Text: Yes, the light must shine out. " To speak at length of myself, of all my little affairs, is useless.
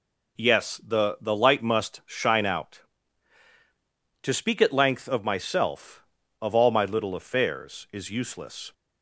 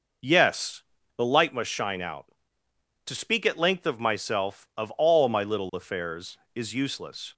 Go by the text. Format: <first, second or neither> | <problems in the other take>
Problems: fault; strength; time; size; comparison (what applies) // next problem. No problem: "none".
second | says "the" twice; at 1.2 s